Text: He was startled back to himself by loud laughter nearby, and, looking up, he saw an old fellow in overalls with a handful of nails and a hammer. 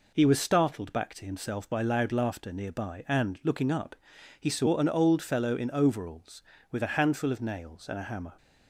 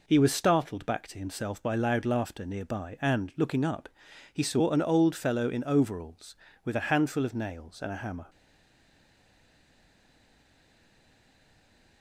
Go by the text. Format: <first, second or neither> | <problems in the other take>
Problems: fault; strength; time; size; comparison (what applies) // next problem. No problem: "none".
first | stays silent after the last word; strong; from 8.2 s on; 3.8 s long